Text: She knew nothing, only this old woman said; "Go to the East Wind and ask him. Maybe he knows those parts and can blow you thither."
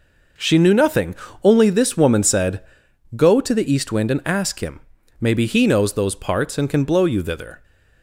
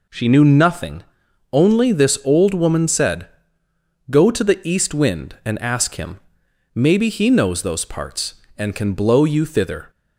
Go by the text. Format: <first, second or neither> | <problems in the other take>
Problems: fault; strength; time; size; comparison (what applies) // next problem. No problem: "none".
second | skips "old"; at 1.9 s